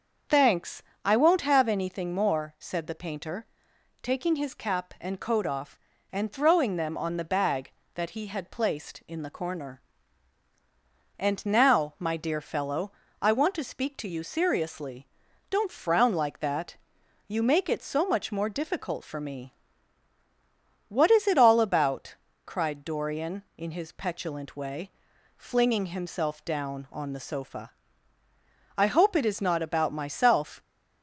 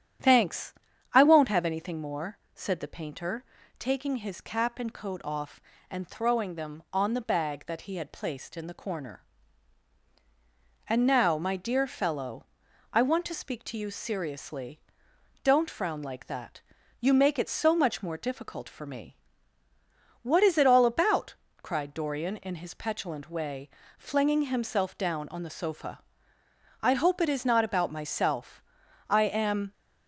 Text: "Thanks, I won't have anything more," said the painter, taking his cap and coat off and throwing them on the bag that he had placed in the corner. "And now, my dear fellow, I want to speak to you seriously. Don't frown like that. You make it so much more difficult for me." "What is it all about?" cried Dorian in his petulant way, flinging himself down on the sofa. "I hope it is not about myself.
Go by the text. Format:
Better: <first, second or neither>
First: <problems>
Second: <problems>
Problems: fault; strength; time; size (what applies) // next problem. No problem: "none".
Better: first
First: starts louder than the rest; until 1.5 s; 7 dB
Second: starts louder than the rest; strong; until 1.6 s; 9.5 dB // goes on to say "I am"; noticeable; from 29.0 s on; 0.64 s long